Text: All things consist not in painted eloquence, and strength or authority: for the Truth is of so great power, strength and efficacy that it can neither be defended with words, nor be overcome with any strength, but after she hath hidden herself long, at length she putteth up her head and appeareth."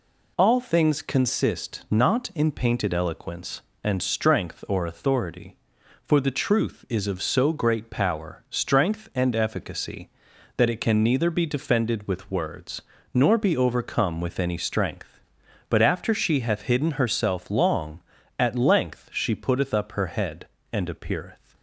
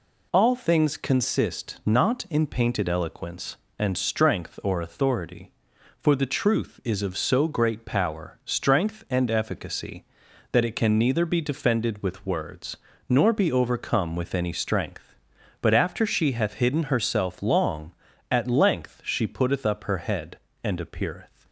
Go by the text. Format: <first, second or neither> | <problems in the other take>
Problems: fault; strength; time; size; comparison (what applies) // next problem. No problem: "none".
neither | none